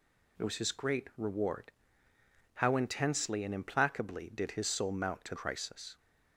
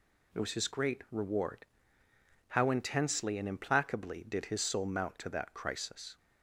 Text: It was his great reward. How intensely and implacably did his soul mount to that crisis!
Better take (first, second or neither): second